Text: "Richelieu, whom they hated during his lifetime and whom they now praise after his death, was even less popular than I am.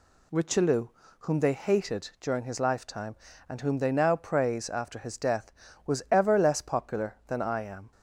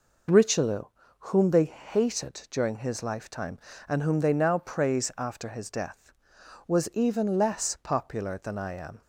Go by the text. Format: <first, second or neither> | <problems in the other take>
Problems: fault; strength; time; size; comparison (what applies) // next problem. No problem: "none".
second | says "ever" for "even"; at 6.0 s